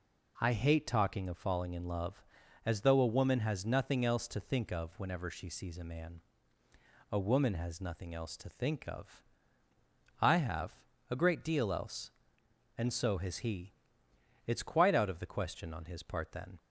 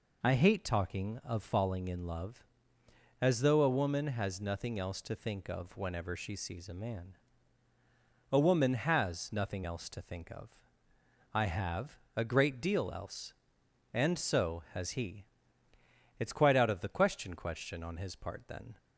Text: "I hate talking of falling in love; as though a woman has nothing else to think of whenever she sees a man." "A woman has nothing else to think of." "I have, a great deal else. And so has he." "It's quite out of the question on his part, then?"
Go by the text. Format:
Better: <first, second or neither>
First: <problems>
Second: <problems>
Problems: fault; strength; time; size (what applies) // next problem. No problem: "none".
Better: first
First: none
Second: says "question" twice; at 17.3 s